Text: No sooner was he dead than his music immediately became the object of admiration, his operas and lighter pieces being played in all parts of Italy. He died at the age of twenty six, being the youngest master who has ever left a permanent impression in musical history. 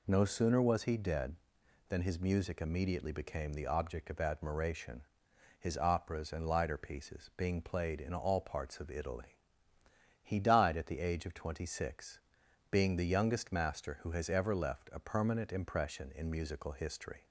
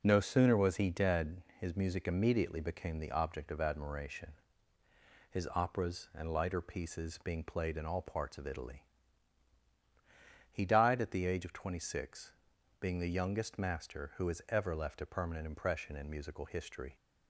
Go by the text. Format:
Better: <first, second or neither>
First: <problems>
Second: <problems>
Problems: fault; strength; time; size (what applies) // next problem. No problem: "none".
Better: first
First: none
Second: skips "than"; at 1.5 s